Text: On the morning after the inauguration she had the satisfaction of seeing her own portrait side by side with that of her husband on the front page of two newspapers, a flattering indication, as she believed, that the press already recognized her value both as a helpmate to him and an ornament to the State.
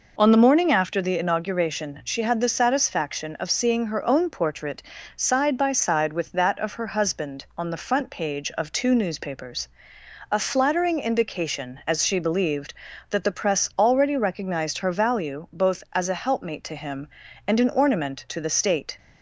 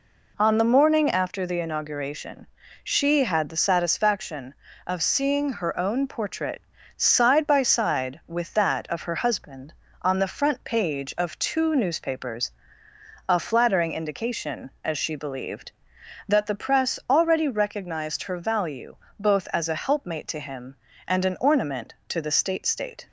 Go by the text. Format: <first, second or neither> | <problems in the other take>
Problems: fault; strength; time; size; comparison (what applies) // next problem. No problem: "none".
first | pauses between "inauguration" and "she"; slight; at 2.4 s; 0.34 s long // pauses between "portrait" and "side"; slight; at 6.6 s; 0.36 s long; slight in the first // pauses between "value" and "both"; slight; at 18.9 s; 0.24 s long // says "State" twice; at 22.6 s